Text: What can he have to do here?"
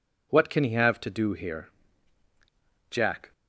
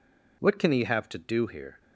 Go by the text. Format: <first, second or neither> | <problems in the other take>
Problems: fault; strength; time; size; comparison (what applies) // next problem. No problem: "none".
second | goes on to say "Jack"; slight; from 2.8 s on; 0.44 s long